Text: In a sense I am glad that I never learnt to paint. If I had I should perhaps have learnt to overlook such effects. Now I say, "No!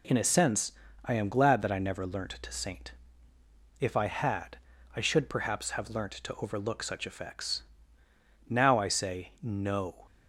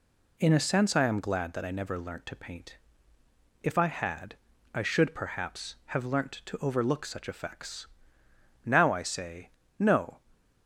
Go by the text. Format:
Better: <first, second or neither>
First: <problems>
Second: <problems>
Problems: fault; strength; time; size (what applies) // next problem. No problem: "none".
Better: second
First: pauses between "sense" and "I"; slight; at 0.7 s; 0.32 s long // says "saint" for "paint"; at 2.5 s // pauses between "had" and "I"; at 4.5 s; 0.38 s long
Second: pauses between "had" and "I"; slight; at 4.3 s; 0.36 s long